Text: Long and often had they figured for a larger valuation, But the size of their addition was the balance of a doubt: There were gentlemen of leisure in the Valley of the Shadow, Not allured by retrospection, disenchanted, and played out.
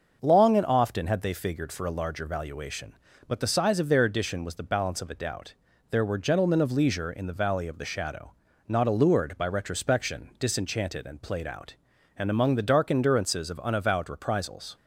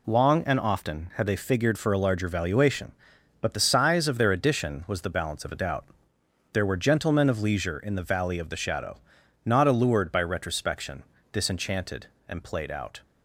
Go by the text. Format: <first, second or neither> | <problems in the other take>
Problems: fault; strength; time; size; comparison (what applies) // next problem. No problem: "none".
second | starts louder than the rest; until 1.2 s; 6 dB // goes on to say "And among the dark endurances of unavowed reprisals"; strong; from 12.1 s on; 2.5 s long